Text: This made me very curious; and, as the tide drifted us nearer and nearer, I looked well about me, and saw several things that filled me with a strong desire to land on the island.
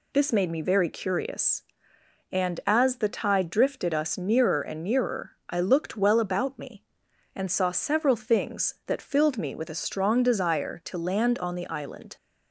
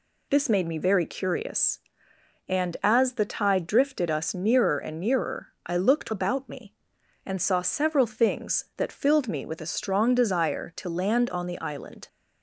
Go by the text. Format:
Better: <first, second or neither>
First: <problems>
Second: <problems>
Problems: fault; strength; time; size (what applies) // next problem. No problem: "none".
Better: first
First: none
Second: skips "well"; at 6.1 s